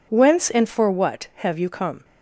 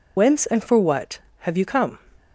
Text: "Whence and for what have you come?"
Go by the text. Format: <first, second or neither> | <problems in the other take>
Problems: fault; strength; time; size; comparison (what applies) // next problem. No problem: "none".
first | loses the start of "Whence"; at 0.1 s; 85 ms